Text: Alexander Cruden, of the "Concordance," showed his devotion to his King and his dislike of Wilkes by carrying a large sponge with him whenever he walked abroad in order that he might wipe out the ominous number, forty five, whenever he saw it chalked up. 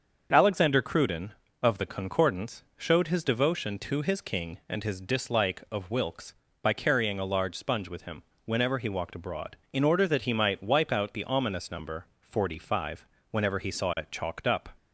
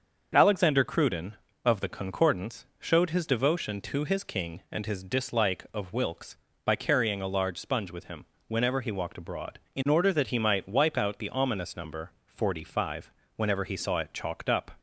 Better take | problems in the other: neither | starts louder than the rest; the same in both // pauses between "him" and "whenever"; slight; the same in both

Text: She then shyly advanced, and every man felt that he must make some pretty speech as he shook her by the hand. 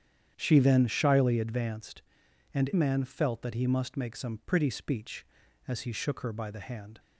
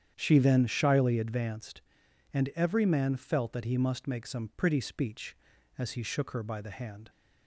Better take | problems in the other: second | starts louder than the rest; strong; until 1.3 s; 9 dB; strong in the second // skips "every"; at 2.7 s

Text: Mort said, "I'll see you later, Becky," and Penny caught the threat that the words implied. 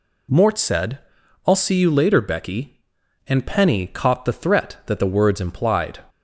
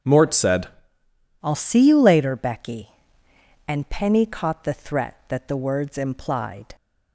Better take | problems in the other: first | starts louder than the rest; strong; until 1.8 s; 7.5 dB // changes voice at "I'll"; from 1.4 s on; 5.3 s long

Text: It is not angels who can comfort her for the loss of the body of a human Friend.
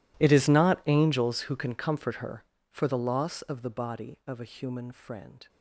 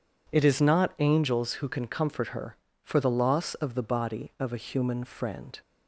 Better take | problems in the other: second | gets quieter; strong; throughout; 22.5 dB

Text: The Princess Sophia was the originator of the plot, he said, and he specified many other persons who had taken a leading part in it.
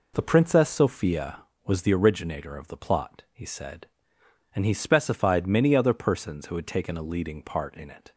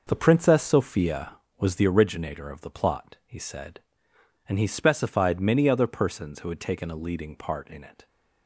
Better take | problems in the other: first | gets quieter; strong; throughout; 8.5 dB

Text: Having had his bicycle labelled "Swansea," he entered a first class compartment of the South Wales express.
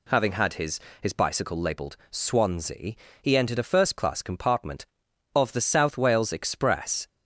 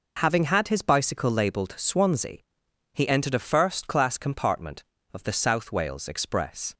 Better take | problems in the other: second | says "his" twice; at 1.0 s

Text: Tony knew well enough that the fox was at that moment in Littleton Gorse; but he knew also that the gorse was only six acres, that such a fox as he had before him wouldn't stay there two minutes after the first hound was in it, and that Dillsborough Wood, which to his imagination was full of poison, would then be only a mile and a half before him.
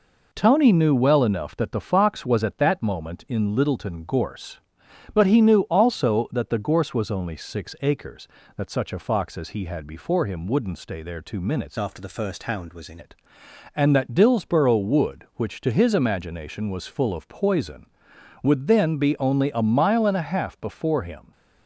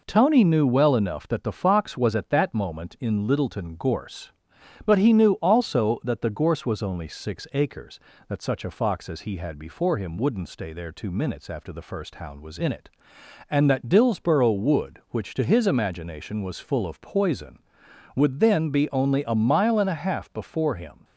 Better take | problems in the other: second | changes voice from "after" to "in"; from 11.7 to 12.9 s; 1.2 s long

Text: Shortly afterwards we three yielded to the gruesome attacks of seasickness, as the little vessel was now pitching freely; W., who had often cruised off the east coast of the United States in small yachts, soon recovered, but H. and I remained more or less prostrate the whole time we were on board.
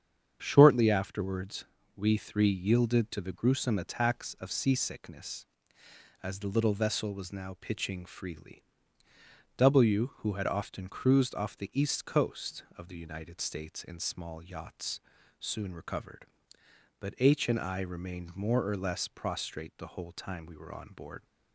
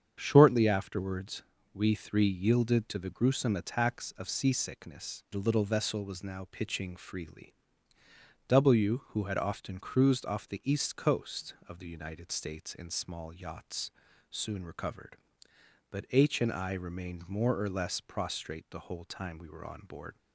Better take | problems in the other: first | starts louder than the rest; strong; until 1.2 s; 7.5 dB; strong in the first // pauses between "afterwards" and "we"; slight; at 1.4 s; 0.30 s long; slight in the first // skips "as"; at 5.2 s

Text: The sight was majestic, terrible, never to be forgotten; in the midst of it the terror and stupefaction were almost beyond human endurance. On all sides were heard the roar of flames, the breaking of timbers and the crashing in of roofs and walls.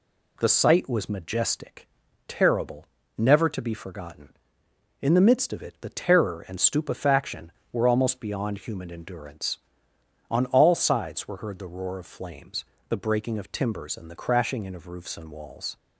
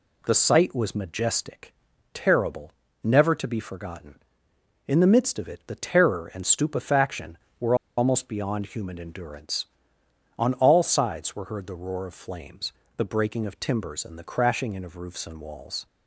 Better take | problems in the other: first | pauses between "were" and "almost"; slight; at 7.7 s; 0.22 s long

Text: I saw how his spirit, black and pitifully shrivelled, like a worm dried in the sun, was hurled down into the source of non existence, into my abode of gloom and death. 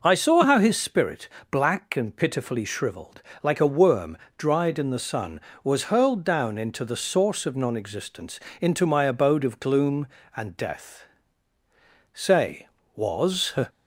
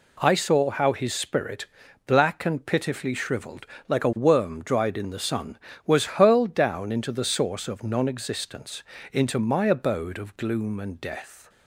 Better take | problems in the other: second | pauses between "worm" and "dried"; slight; at 4.1 s; 0.22 s long // goes on to say "Say was"; from 12.1 s on; 1.4 s long

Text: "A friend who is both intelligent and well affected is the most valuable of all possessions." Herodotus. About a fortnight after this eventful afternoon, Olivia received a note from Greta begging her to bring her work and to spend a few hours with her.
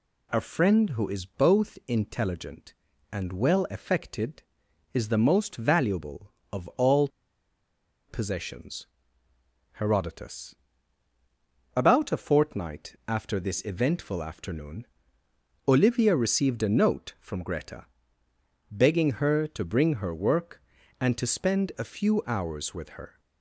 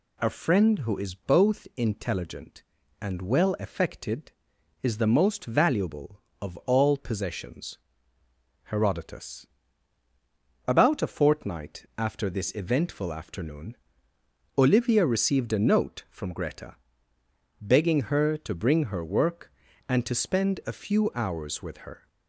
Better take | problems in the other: second | pauses between "all" and "possessions"; at 7.0 s; 1.0 s long // pauses between "Greta" and "begging"; noticeable; at 17.8 s; 0.84 s long; noticeable in the second

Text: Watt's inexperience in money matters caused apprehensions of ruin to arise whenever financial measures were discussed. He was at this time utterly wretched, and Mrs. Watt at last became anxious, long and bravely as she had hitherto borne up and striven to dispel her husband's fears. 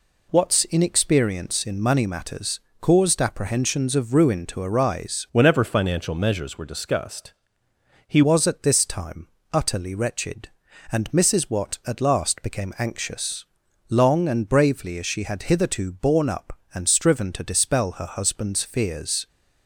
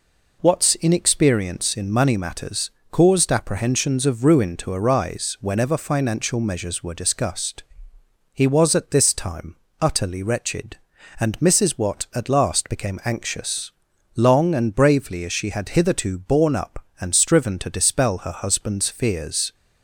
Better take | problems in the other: second | pauses between "matters" and "caused"; slight; at 2.5 s; 0.22 s long; slight in the second // changes voice from "whenever" to "He"; from 5.3 to 8.2 s; 2.9 s long // pauses between "time" and "utterly"; slight; at 9.2 s; 0.26 s long; slight in the second

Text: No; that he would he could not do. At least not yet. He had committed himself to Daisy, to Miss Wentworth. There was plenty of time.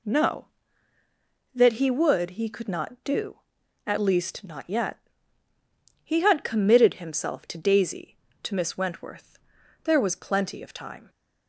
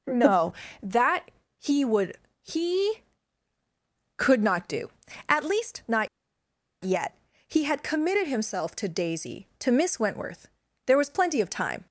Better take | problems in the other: first | pauses between "that" and "he"; slight; at 1.3 s; 0.28 s long // pauses between "would" and "he"; slight; at 2.1 s; 0.24 s long // pauses between "not" and "yet"; noticeable; at 6.0 s; 0.76 s long

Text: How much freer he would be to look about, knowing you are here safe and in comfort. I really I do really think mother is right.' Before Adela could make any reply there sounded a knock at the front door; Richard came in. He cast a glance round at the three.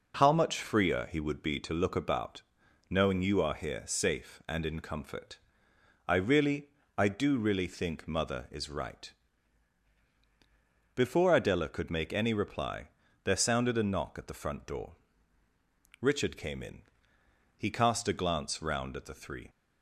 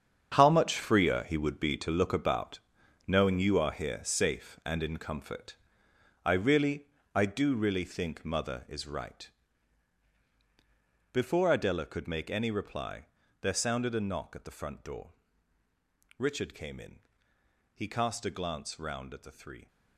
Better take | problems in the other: first | gets quieter; strong; throughout; 12 dB // pauses between "really" and "I"; slight; at 6.8 s; 0.28 s long; slight in the first // pauses between "reply" and "there"; at 13.0 s; 0.38 s long; also in the first

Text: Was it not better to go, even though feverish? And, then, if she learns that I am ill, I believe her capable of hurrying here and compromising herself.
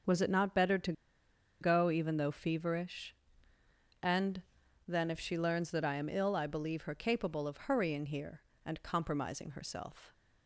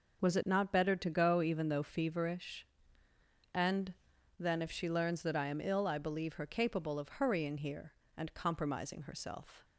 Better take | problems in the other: second | starts louder than the rest; until 1.7 s; 6 dB; noticeable in the second // pauses between "to" and "go"; noticeable; at 0.9 s; 0.68 s long

